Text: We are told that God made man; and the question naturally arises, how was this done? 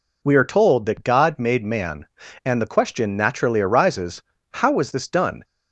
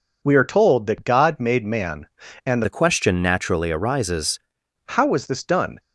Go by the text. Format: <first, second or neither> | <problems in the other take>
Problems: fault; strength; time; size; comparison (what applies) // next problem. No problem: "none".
first | changes voice from "the" to "arises"; from 2.6 to 4.3 s; 1.7 s long